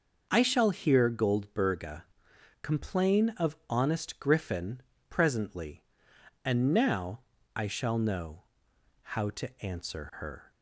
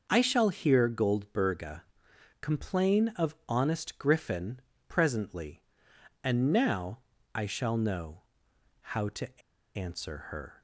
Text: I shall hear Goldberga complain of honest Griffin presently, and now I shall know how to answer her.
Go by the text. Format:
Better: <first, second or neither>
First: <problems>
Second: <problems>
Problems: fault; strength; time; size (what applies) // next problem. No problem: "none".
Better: first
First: pauses between "Goldberga" and "complain"; noticeable; at 2.0 s; 0.60 s long // pauses between "Griffin" and "presently"; slight; at 4.8 s; 0.28 s long // pauses between "now" and "I"; slight; at 7.2 s; 0.34 s long // pauses between "know" and "how"; noticeable; at 8.4 s; 0.60 s long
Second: pauses between "Goldberga" and "complain"; noticeable; at 1.8 s; 0.60 s long // pauses between "Griffin" and "presently"; slight; at 4.5 s; 0.28 s long // pauses between "now" and "I"; slight; at 6.9 s; 0.34 s long // pauses between "know" and "how"; noticeable; at 8.2 s; 0.60 s long // pauses between "to" and "answer"; slight; at 9.4 s; 0.36 s long